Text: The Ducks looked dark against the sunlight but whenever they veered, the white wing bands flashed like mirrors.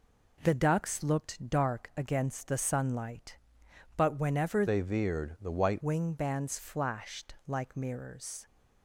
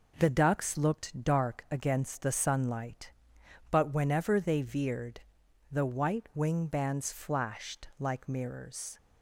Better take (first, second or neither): second